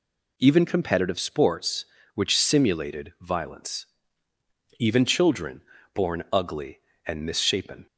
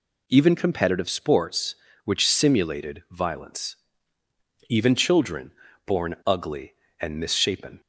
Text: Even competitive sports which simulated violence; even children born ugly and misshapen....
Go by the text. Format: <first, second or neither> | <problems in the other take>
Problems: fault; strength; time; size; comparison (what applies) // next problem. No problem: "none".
neither | pauses between "children" and "born"; slight; the same in both